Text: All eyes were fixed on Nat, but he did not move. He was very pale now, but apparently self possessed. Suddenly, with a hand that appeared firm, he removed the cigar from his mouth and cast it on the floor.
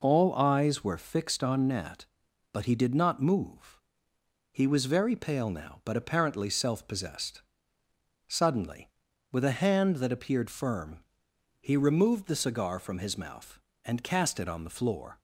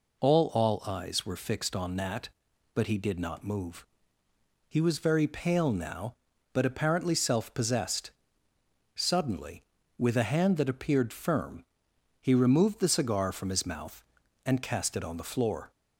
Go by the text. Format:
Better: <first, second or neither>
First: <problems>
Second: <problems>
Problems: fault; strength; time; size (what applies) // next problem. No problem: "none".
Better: first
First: none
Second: says "All" twice; at 0.5 s